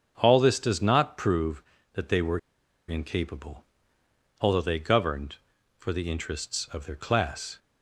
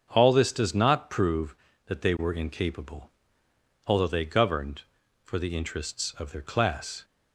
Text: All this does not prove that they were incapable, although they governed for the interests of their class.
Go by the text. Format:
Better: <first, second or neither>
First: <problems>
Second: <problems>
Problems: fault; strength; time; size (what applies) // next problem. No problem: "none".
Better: second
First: starts louder than the rest; until 1.1 s; 7 dB // pauses between "were" and "incapable"; noticeable; at 2.3 s; 0.50 s long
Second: starts louder than the rest; until 1.1 s; 7 dB